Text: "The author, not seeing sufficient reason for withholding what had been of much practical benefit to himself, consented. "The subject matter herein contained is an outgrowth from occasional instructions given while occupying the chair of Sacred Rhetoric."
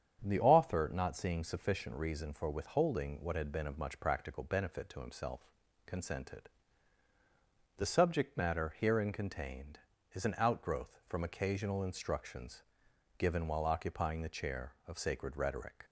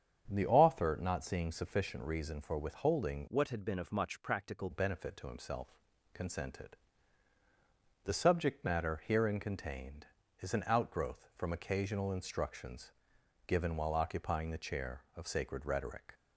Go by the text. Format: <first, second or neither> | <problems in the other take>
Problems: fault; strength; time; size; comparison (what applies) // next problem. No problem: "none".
first | starts louder than the rest; strong; until 1.2 s; 8 dB; strong in the first // changes voice from "what" to "practical"; from 3.2 to 4.6 s; 1.4 s long // pauses between "instructions" and "given"; noticeable; at 12.9 s; 0.56 s long; noticeable in the first